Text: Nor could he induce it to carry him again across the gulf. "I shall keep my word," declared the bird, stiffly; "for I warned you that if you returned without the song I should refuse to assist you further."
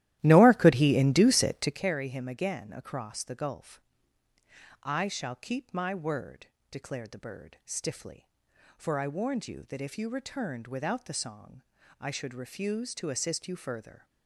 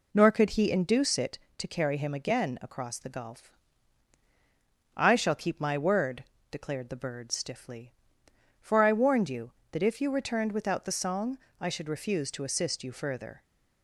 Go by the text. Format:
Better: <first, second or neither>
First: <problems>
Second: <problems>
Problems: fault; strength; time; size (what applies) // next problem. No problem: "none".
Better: second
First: starts louder than the rest; strong; until 1.8 s; 14 dB // pauses between "song" and "I"; at 11.6 s; 0.40 s long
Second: pauses between "song" and "I"; slight; at 11.3 s; 0.22 s long